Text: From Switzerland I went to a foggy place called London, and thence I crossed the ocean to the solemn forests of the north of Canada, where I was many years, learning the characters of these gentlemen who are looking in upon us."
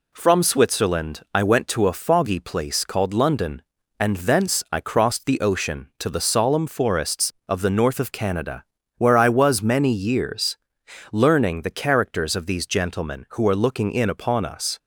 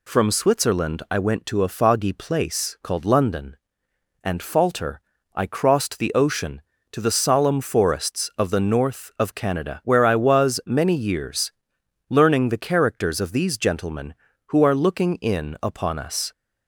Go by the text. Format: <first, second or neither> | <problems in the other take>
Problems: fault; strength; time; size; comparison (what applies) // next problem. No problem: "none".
first | says "falter" for "thence"; at 4.4 s